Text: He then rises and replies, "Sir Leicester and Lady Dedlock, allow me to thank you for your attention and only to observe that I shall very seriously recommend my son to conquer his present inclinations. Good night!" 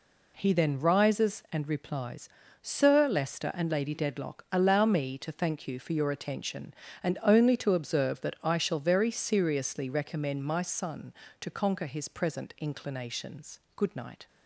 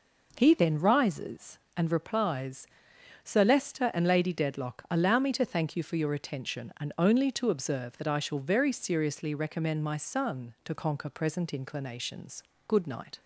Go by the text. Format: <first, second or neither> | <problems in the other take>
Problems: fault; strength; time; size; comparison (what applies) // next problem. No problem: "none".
first | skips "his"; at 11.0 s